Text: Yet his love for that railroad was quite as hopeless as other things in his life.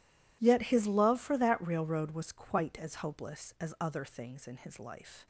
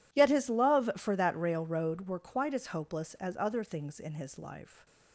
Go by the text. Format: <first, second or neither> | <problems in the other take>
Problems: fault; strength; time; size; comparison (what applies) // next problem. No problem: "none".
first | says "were" for "was"; at 2.0 s // stays silent after the last word; slight; from 4.6 s on; 0.5 s long